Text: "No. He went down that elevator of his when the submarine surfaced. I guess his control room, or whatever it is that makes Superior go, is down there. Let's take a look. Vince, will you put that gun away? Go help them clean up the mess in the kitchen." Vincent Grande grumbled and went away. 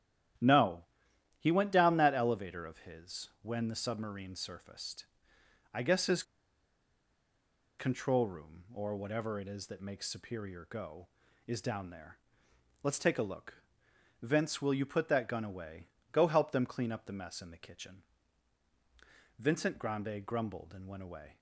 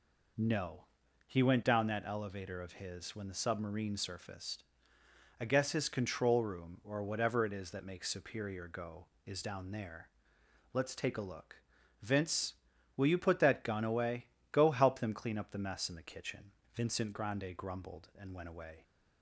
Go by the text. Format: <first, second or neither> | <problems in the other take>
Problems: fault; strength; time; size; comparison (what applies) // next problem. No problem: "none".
second | starts louder than the rest; strong; until 1.9 s; 11 dB // pauses between "his" and "control"; strong; at 6.2 s; 1.5 s long